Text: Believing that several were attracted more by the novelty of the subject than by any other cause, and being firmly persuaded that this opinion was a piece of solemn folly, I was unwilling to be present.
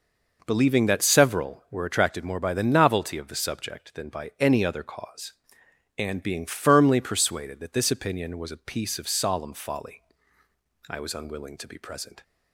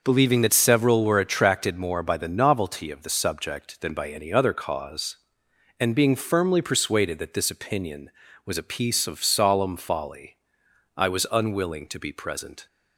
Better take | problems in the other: neither | none

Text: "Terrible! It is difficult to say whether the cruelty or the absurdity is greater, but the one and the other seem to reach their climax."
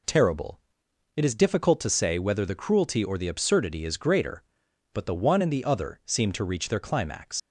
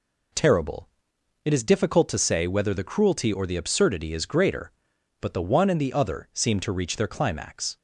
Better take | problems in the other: second | leaves "climax" unfinished; at 7.3 s; 105 ms

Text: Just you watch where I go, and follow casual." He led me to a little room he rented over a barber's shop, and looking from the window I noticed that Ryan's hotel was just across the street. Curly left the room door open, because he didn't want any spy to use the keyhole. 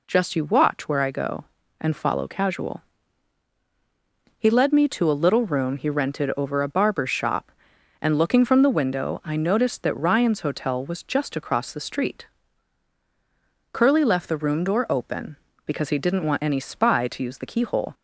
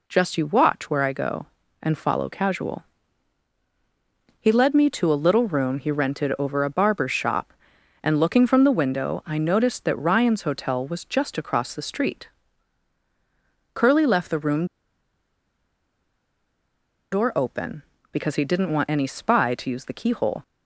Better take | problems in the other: first | pauses between "room" and "door"; strong; at 14.6 s; 2.4 s long

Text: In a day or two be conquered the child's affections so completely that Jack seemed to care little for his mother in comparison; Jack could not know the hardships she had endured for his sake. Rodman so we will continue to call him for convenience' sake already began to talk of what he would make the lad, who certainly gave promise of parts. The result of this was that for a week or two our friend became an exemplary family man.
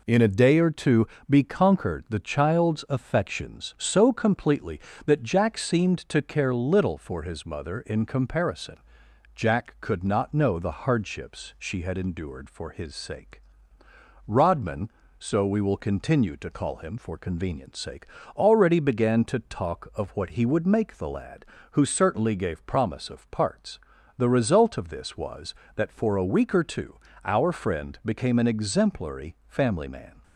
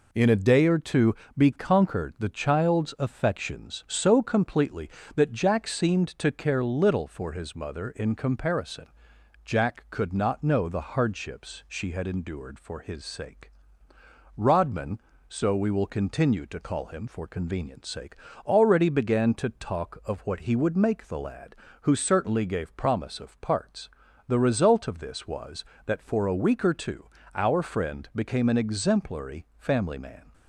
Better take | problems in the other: neither | pauses between "two" and "be"; slight; the same in both // pauses between "sake" and "already"; slight; the same in both // pauses between "two" and "our"; slight; the same in both

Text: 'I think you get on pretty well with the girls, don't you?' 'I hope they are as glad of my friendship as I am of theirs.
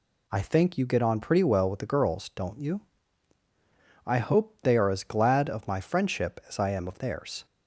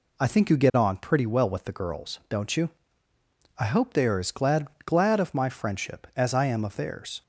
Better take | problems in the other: first | says "glad" twice; at 4.8 s

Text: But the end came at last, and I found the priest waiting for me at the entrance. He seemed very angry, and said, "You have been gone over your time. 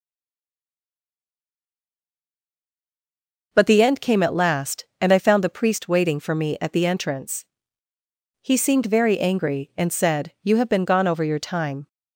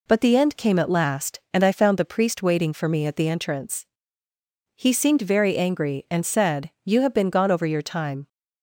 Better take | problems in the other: second | stays silent before the first word; strong; until 3.5 s; 3.5 s long

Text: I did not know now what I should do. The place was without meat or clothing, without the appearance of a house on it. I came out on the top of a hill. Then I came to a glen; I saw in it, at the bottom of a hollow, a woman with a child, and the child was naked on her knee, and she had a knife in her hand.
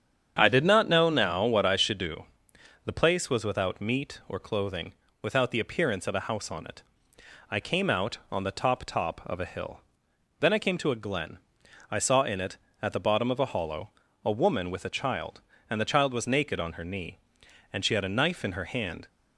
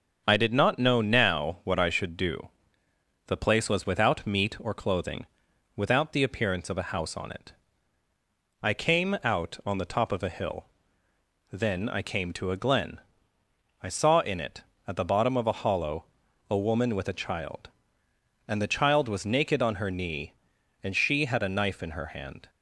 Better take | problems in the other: second | starts louder than the rest; strong; until 1.4 s; 8 dB; also in the second // says "top" twice; at 8.8 s

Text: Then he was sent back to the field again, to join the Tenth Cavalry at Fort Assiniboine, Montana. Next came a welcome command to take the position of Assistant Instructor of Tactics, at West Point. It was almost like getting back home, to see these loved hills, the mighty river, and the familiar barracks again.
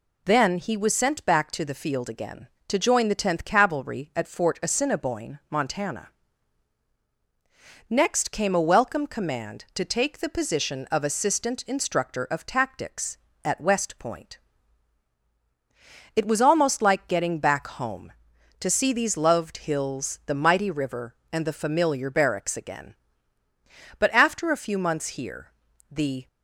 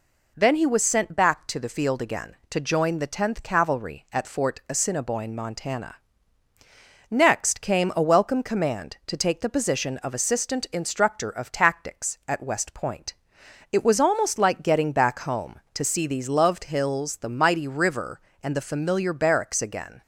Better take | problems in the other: second | goes on to say "But after a few months here the"; strong; from 23.9 s on; 2.3 s long

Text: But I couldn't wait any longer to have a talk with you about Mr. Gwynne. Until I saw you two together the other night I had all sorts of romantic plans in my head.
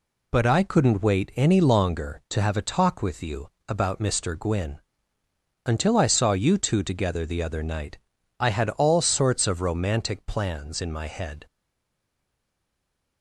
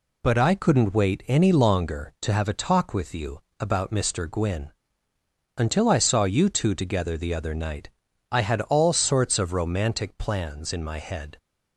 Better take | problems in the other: second | pauses between "you" and "about"; slight; at 3.4 s; 0.18 s long; slight in the second // pauses between "night" and "I"; at 7.9 s; 0.40 s long; also in the second // stays silent after the last word; noticeable; from 11.4 s on; 1.8 s long

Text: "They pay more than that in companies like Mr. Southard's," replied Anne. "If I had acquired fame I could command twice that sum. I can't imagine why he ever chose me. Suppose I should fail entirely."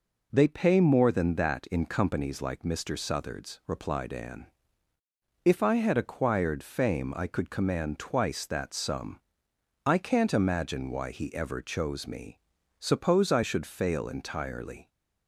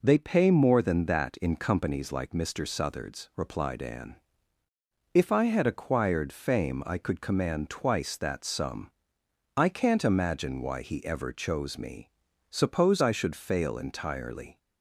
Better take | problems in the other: neither | none

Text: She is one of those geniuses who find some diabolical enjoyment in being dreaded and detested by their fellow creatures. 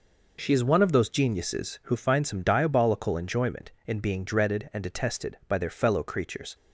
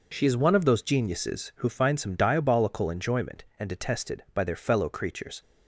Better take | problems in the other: first | skips "in being dreaded"; at 3.5 s

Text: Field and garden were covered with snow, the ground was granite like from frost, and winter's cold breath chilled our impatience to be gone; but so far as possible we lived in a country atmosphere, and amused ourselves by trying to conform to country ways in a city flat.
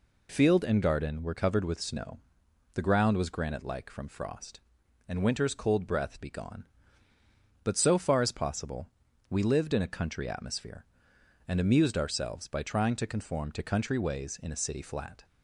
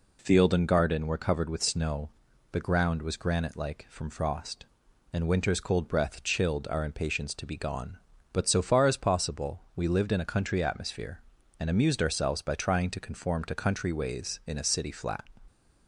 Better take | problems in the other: second | skips "chilled our impatience to"; at 6.2 s // pauses between "possible" and "we"; at 8.8 s; 0.40 s long; slight in the second

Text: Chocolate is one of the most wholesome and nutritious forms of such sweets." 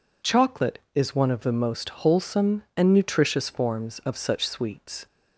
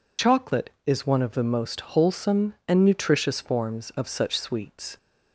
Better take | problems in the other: first | loses the start of "Chocolate"; at 0.1 s; 40 ms

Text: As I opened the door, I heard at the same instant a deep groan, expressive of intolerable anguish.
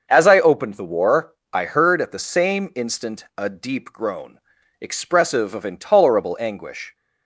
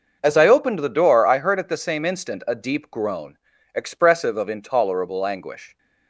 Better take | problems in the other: second | starts louder than the rest; until 1.1 s; 6.5 dB; noticeable in the second // says "war" for "door"; at 0.8 s

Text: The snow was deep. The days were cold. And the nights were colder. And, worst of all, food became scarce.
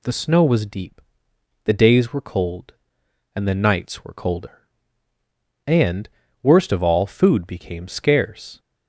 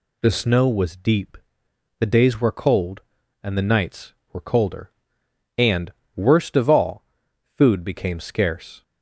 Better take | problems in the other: neither | none

